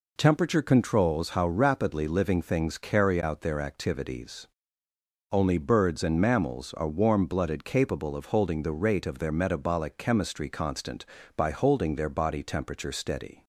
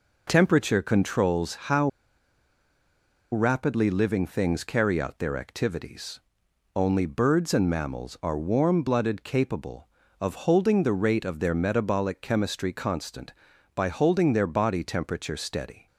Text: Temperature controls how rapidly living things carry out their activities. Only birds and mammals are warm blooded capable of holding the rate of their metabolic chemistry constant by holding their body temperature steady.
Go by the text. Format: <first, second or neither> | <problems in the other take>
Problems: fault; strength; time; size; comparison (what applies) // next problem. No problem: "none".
first | pauses between "how" and "rapidly"; strong; at 1.8 s; 1.4 s long